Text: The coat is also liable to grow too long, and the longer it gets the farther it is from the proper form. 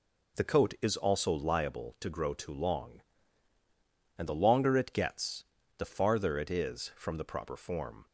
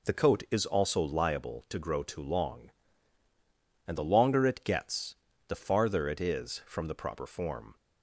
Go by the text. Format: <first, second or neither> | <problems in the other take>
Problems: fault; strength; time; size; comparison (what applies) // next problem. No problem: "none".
neither | pauses between "gets" and "the"; slight; the same in both